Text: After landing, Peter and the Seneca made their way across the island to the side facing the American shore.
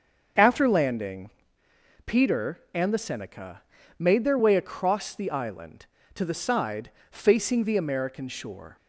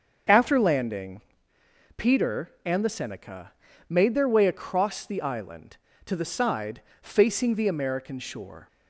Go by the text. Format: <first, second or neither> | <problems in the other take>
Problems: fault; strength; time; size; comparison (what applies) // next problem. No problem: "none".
neither | starts louder than the rest; the same in both // pauses between "Seneca" and "made"; slight; the same in both // pauses between "side" and "facing"; slight; the same in both